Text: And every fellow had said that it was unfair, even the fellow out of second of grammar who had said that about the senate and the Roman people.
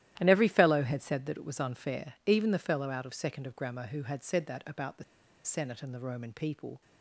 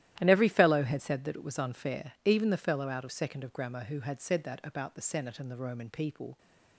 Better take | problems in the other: second | starts louder than the rest; strong; until 1.1 s; 13.5 dB; strong in the second // pauses between "the" and "senate"; at 5.0 s; 0.40 s long

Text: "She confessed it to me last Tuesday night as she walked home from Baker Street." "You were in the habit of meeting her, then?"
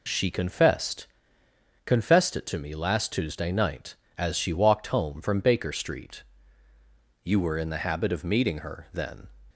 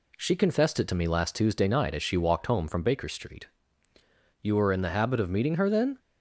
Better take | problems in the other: second | says "confessed" twice; at 1.8 s

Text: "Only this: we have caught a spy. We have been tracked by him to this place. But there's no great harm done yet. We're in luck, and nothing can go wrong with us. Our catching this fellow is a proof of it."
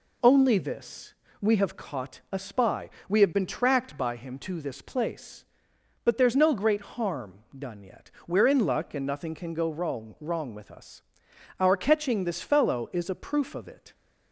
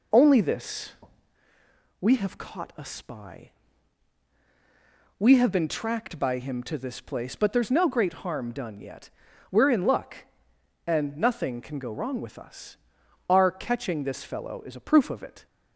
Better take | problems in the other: second | pauses between "harm" and "done"; slight; at 7.3 s; 0.18 s long // says "wrong" twice; at 10.1 s

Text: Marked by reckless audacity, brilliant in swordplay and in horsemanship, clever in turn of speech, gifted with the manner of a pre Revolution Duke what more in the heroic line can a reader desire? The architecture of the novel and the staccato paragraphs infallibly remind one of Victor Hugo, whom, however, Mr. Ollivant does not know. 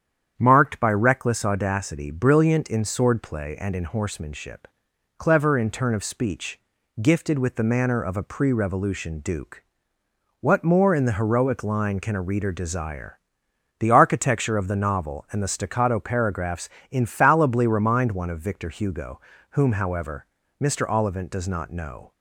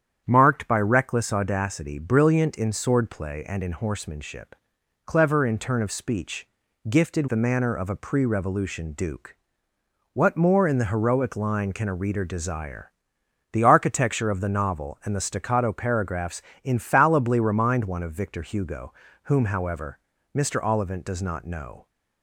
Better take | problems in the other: first | starts louder than the rest; strong; until 1.2 s; 9 dB; strong in the first // skips "with"; at 7.2 s // pauses between "Duke" and "what"; noticeable; at 9.3 s; 0.80 s long; noticeable in the first // pauses between "paragraphs" and "infallibly"; slight; at 16.4 s; 0.22 s long; slight in the first

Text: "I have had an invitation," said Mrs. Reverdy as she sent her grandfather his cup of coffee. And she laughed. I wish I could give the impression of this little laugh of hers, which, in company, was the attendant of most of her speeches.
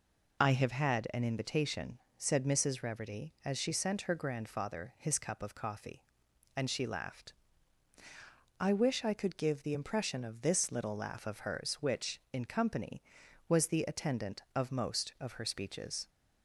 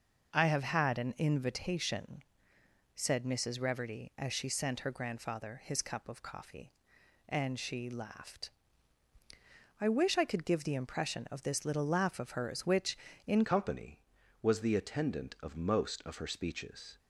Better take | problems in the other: first | changes voice at "company"; from 13.4 s on; 3.5 s long

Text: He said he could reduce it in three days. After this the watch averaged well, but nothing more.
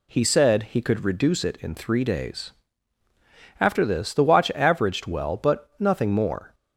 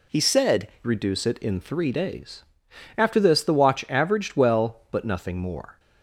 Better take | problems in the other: first | skips "he could"; at 0.7 s

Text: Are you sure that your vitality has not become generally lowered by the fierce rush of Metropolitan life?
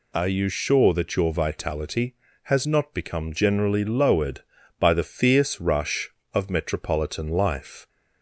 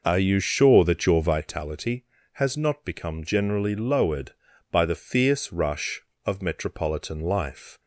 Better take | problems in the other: first | starts louder than the rest; noticeable; until 1.4 s; 5.5 dB

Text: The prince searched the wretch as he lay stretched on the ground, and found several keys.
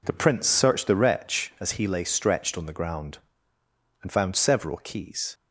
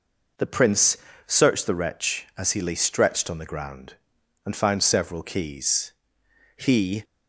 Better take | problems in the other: first | pauses between "prince" and "searched"; slight; at 0.9 s; 0.28 s long // goes on to say "He"; slight; from 6.5 s on; 0.48 s long

